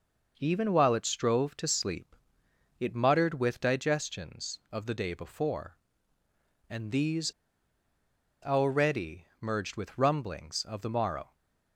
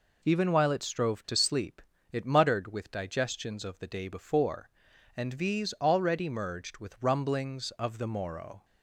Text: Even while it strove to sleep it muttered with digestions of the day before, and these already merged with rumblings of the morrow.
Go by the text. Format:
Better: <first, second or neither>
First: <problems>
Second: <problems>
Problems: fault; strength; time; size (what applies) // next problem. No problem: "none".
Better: second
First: pauses between "sleep" and "it"; noticeable; at 2.1 s; 0.64 s long // pauses between "these" and "already"; at 7.3 s; 1.1 s long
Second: pauses between "sleep" and "it"; slight; at 1.8 s; 0.28 s long